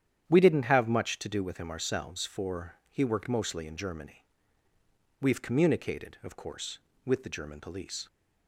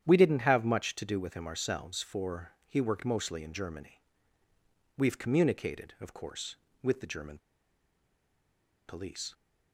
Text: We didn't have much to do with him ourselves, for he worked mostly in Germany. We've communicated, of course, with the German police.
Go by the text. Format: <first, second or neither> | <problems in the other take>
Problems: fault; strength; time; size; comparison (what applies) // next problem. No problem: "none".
first | starts louder than the rest; strong; until 1.0 s; 9.5 dB; strong in the first // pauses between "German" and "police"; strong; at 7.3 s; 1.4 s long